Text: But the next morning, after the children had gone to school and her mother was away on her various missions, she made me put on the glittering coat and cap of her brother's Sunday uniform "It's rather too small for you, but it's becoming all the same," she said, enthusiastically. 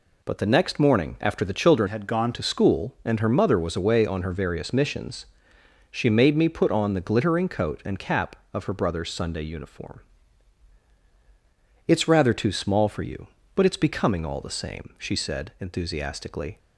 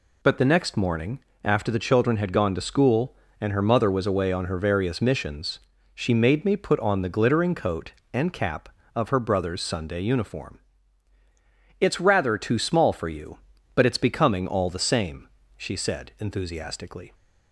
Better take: second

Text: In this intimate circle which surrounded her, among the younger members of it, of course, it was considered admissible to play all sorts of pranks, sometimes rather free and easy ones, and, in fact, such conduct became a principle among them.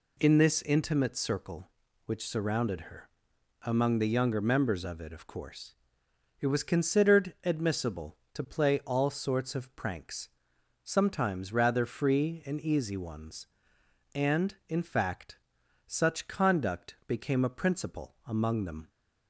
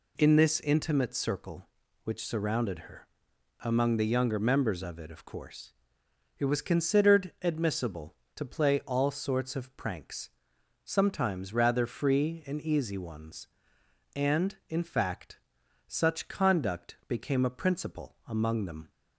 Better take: neither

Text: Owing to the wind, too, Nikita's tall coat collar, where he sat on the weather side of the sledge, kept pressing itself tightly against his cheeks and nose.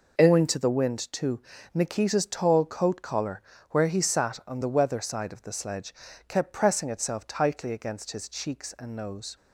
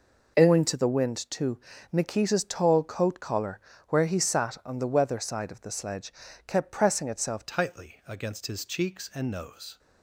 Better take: first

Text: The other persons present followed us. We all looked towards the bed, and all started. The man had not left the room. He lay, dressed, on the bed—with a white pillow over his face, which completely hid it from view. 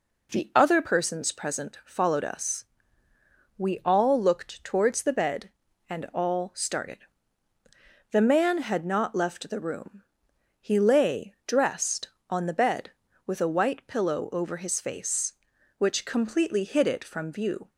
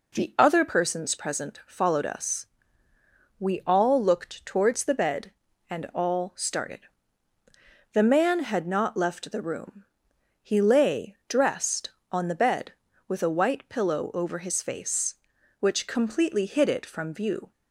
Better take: neither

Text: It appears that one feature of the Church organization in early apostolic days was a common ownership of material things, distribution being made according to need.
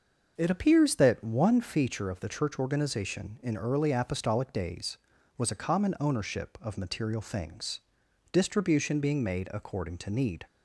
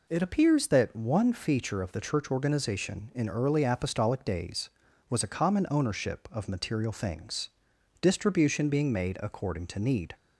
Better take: second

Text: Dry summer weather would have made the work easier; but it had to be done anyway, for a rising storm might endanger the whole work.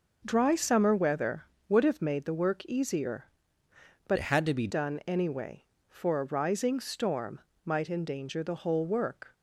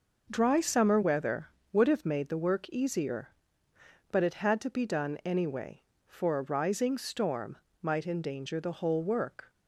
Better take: second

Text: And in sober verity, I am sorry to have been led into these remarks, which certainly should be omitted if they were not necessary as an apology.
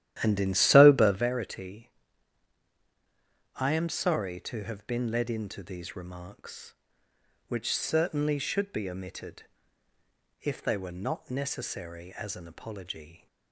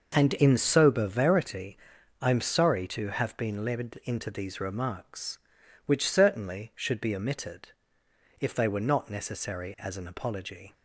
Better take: second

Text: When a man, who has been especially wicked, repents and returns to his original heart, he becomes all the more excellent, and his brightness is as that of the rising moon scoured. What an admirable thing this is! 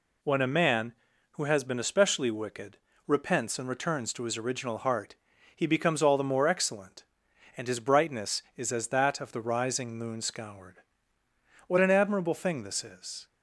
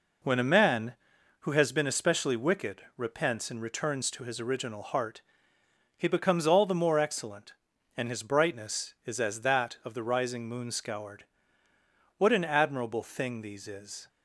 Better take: first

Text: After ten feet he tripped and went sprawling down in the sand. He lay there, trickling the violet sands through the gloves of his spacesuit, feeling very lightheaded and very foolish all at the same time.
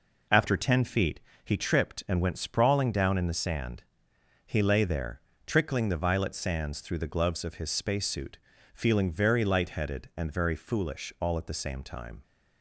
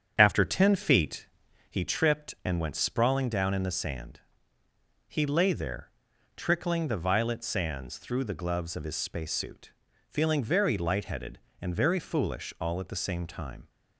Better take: first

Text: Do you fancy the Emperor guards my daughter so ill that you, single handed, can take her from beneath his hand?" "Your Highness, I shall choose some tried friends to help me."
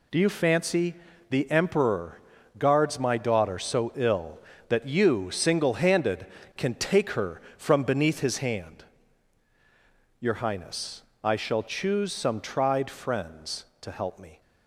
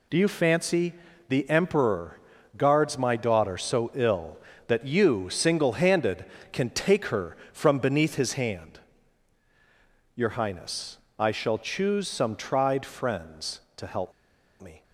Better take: first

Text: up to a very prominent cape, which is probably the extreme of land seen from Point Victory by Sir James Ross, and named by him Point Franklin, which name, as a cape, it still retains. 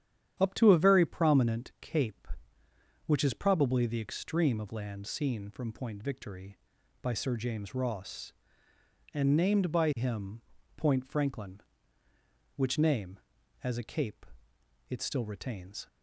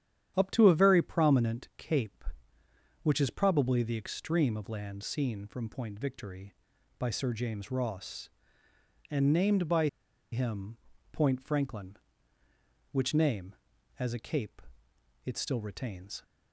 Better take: first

